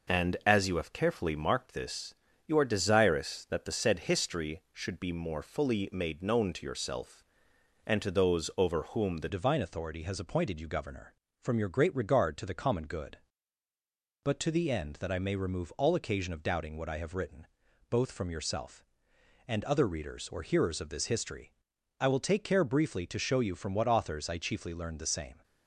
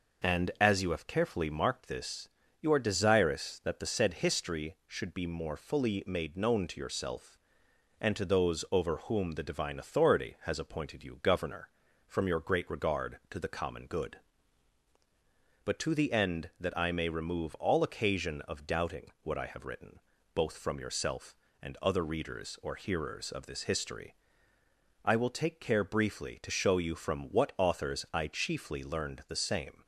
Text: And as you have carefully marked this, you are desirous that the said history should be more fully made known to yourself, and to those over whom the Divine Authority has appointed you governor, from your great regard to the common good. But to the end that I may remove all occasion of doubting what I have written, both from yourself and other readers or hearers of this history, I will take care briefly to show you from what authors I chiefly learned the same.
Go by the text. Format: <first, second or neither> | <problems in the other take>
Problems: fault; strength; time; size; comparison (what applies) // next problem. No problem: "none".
second | changes voice at "Divine"; from 9.2 s on; 16.2 s long